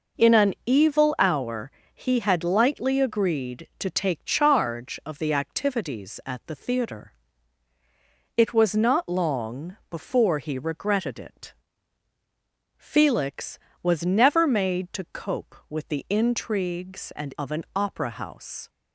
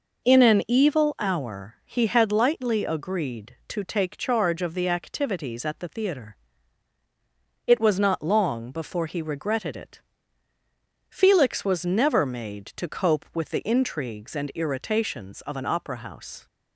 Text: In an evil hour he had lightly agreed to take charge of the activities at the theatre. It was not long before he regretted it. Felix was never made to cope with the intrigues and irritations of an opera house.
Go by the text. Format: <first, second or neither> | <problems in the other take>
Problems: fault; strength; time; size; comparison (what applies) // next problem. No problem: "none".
second | pauses between "hour" and "he"; slight; at 1.7 s; 0.22 s long // skips "irritations"; at 17.3 s